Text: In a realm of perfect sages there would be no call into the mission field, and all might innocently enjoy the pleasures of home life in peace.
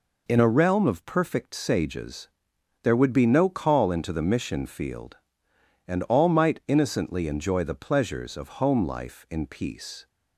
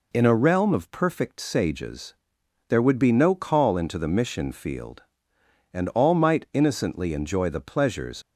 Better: first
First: pauses between "sages" and "there"; noticeable; at 2.2 s; 0.52 s long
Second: pauses between "sages" and "there"; noticeable; at 2.1 s; 0.52 s long // stops before "of home life in peace"; at 8.2 s

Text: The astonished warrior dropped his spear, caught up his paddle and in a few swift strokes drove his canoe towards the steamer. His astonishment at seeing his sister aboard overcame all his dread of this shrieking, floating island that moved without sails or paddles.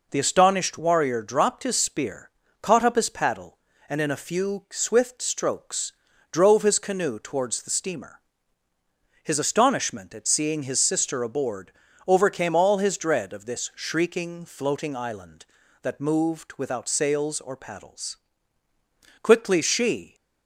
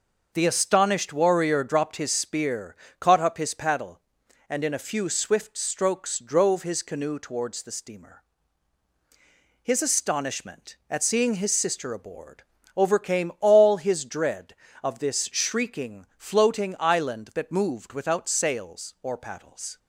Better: second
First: pauses between "strokes" and "drove"; at 5.9 s; 0.38 s long // pauses between "aboard" and "overcame"; slight; at 11.7 s; 0.36 s long // goes on to say "Quickly she"; noticeable; from 19.2 s on; 0.92 s long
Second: pauses between "aboard" and "overcame"; slight; at 12.4 s; 0.34 s long

